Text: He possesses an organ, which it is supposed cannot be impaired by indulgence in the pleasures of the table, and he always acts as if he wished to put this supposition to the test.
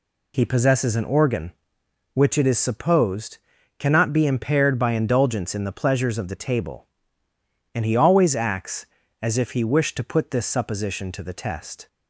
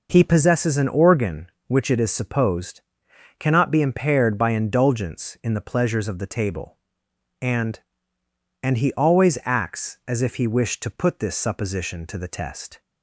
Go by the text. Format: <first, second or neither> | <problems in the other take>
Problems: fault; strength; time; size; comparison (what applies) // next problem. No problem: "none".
first | pauses between "supposed" and "cannot"; noticeable; at 2.8 s; 0.58 s long; also in the first // says "and" twice; at 8.6 s